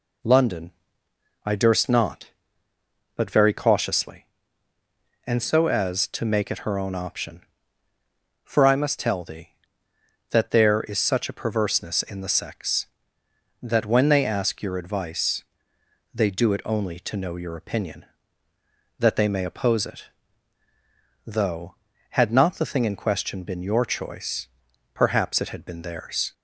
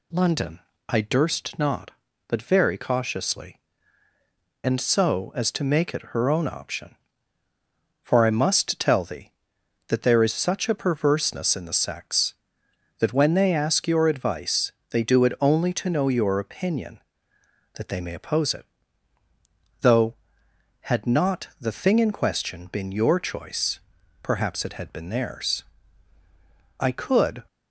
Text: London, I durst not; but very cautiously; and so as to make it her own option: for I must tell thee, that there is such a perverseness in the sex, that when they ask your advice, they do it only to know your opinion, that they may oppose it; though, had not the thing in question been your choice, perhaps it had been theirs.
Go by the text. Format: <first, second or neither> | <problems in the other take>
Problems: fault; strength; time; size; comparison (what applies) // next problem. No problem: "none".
first | goes on to say "I could"; noticeable; from 26.8 s on; 0.62 s long